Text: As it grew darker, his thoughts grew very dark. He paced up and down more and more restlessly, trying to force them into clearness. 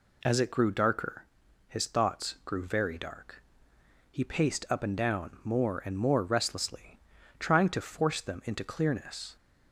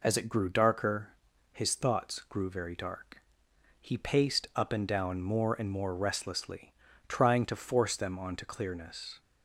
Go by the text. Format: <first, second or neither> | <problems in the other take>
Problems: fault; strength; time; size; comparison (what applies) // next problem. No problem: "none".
first | says "onto" for "into"; at 8.1 s